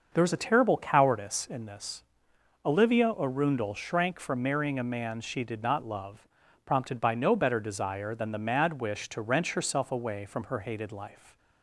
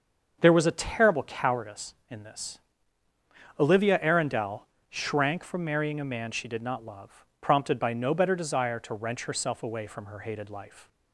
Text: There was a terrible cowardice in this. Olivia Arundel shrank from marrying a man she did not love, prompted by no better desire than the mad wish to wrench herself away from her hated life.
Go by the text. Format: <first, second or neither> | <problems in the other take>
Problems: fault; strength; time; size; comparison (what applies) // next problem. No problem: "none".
first | starts louder than the rest; until 1.4 s; 6.5 dB; also in the first // pauses between "Arundel" and "shrank"; slight; at 4.6 s; 0.22 s long // skips "than the mad wish"; at 8.7 s